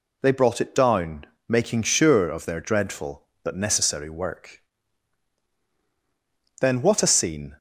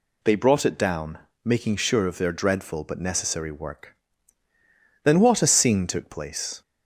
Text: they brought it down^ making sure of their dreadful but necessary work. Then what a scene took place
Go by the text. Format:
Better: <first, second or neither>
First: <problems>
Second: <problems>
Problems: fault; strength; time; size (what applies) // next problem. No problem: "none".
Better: second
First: pauses between "down" and "making"; slight; at 1.2 s; 0.24 s long // stops before "took place"; at 7.5 s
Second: pauses between "down" and "making"; slight; at 1.1 s; 0.24 s long